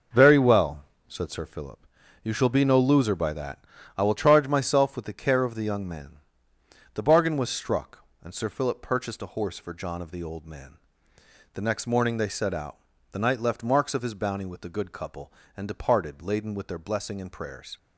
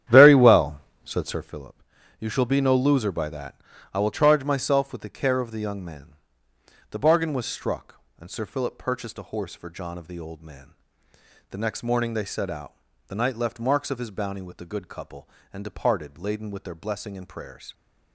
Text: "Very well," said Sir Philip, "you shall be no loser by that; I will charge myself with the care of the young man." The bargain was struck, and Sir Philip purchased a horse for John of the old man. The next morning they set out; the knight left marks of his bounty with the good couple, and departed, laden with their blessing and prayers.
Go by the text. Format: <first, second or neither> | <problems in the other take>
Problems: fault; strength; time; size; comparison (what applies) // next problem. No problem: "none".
first | starts louder than the rest; strong; until 1.6 s; 10.5 dB